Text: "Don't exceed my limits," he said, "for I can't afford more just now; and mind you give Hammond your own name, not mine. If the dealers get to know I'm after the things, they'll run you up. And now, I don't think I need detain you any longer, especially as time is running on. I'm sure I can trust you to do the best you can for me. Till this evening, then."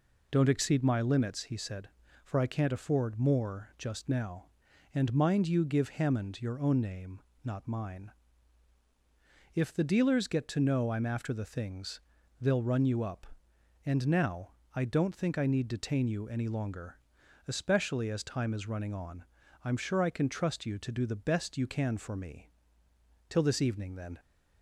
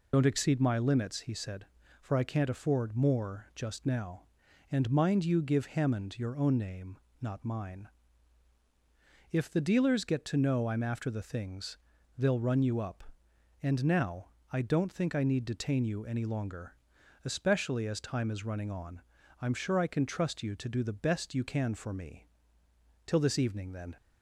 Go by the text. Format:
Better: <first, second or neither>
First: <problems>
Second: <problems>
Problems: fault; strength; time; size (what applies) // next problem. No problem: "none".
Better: first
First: none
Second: loses the start of "Don't"; at 0.1 s; 60 ms